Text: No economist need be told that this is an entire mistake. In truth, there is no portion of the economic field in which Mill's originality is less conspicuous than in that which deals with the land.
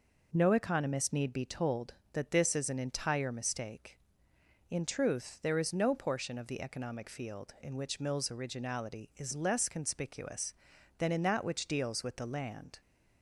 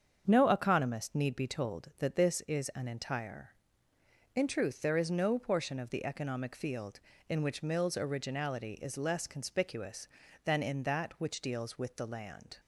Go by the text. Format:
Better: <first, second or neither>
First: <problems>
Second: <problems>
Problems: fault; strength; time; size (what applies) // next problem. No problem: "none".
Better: first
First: none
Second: starts louder than the rest; until 1.2 s; 7 dB // skips "mistake"; at 3.9 s